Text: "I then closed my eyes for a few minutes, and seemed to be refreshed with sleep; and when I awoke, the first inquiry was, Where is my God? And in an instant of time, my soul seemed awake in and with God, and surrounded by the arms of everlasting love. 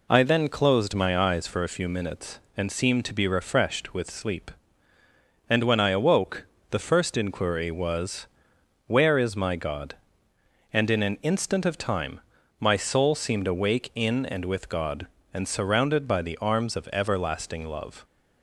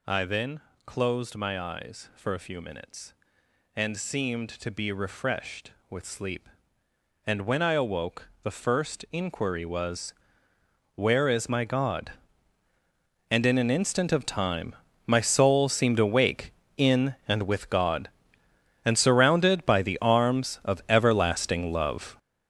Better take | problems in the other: first | gets louder; strong; throughout; 10.5 dB // pauses between "then" and "closed"; slight; at 0.5 s; 0.24 s long

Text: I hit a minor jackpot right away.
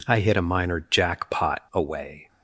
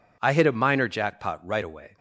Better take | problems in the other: second | skips "right"; at 1.6 s

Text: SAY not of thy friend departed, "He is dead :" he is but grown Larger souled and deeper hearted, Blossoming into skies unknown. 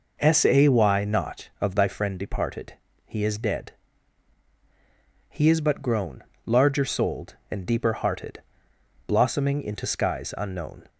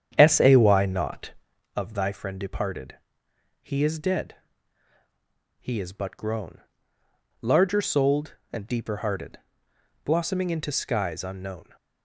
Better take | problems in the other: first | starts louder than the rest; strong; until 1.6 s; 9 dB // pauses between "grown" and "Larger"; noticeable; at 6.6 s; 0.80 s long; slight in the first

